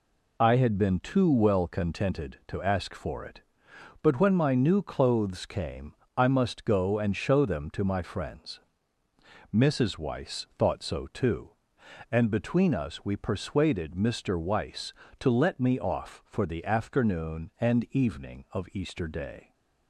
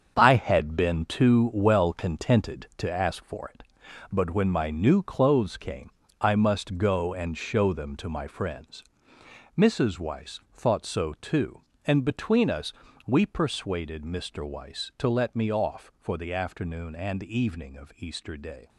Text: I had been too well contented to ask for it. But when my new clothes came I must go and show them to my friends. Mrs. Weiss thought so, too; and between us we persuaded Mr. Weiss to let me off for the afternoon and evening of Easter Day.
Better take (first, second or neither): first